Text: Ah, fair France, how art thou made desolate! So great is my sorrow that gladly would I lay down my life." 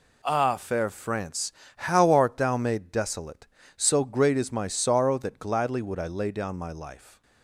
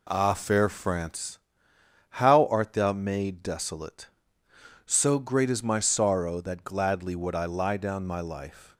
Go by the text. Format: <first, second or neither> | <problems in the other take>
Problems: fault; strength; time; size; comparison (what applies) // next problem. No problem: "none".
first | says "lie" for "lay"; at 7.4 s